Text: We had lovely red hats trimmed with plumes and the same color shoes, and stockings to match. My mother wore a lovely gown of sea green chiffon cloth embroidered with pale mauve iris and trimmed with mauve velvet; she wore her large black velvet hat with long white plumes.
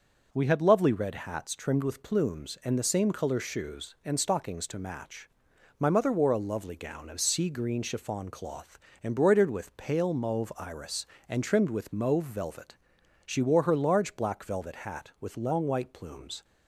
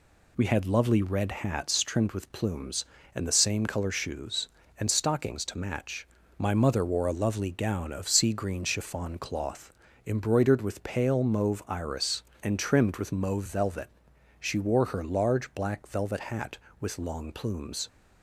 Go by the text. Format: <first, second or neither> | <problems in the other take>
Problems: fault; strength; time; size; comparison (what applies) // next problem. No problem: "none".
first | pauses between "cloth" and "embroidered"; slight; at 9.7 s; 0.34 s long; slight in the first // skips "white"; at 17.3 s